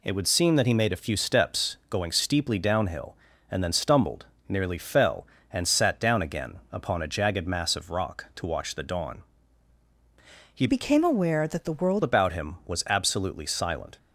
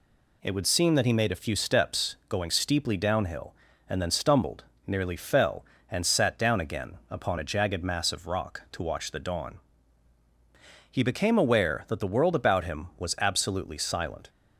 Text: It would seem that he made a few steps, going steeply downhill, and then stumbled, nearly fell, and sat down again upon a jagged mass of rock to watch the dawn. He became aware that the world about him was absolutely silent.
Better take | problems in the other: second | changes voice from "became" to "world"; from 10.6 to 12.0 s; 1.4 s long

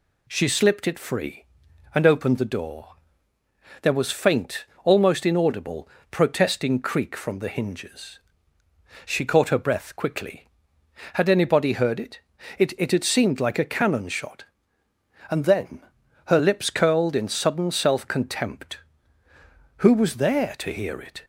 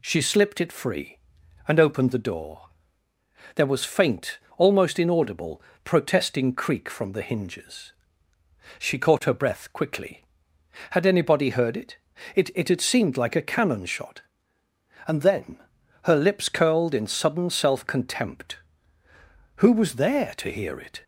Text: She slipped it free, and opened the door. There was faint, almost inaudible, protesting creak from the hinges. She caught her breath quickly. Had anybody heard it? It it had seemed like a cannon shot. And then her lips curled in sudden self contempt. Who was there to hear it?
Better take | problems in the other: neither | pauses between "then" and "her"; noticeable; the same in both

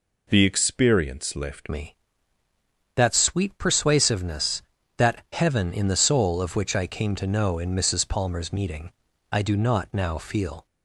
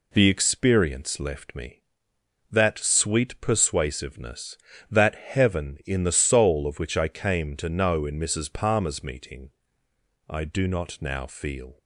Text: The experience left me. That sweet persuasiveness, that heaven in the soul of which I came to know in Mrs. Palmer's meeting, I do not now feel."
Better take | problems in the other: second | changes voice at "me"; from 1.6 s on; 9.0 s long

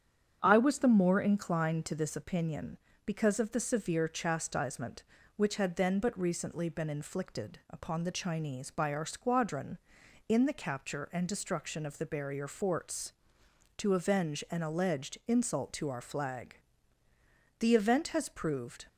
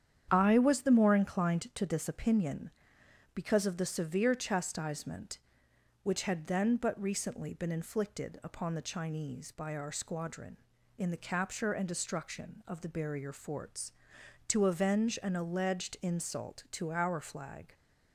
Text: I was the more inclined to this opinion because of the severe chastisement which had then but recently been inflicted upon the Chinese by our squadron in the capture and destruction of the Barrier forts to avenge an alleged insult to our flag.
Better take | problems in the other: second | starts louder than the rest; strong; until 1.4 s; 8.5 dB; strong in the second // goes on to say "The event has proved"; noticeable; from 17.5 s on; 1.2 s long

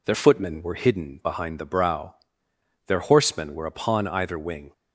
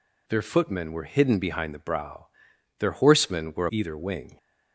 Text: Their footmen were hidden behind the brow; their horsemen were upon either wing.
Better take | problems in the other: first | skips "upon"; at 3.6 s

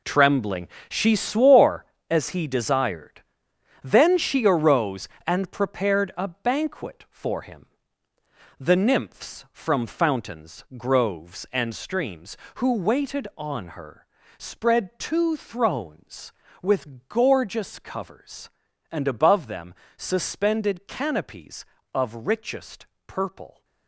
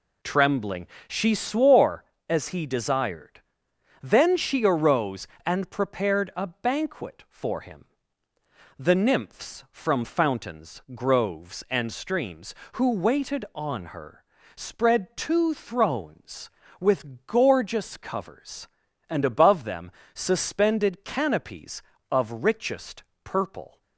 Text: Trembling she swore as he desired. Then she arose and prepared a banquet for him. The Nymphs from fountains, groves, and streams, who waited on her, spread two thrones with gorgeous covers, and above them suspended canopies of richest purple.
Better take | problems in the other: second | gets quieter; strong; throughout; 12 dB // pauses between "Trembling" and "she"; slight; at 0.6 s; 0.22 s long; slight in the second // pauses between "them" and "suspended"; slight; at 19.7 s; 0.22 s long; slight in the second // pauses between "richest" and "purple"; slight; at 22.8 s; 0.20 s long; slight in the second

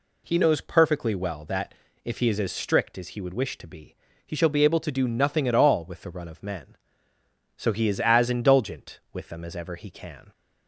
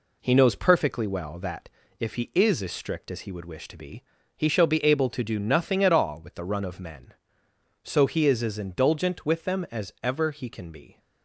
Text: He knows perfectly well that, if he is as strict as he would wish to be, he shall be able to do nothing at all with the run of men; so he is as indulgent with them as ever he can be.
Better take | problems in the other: second | stops before "be"; at 10.3 s

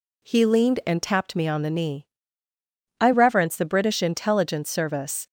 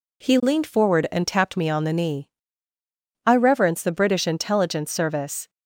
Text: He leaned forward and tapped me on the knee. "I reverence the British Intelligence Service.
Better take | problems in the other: second | skips "forward"; at 0.8 s

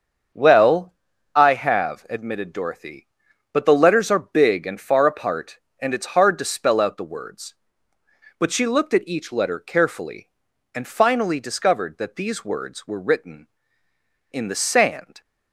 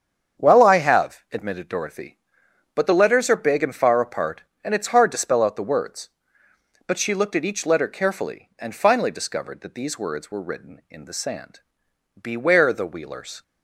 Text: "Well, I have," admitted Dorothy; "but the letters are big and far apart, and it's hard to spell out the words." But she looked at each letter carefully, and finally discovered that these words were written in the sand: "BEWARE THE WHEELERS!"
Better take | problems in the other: second | starts louder than the rest; until 1.7 s; 7 dB; strong in the second // stops before "BEWARE THE WHEELERS"; at 15.2 s

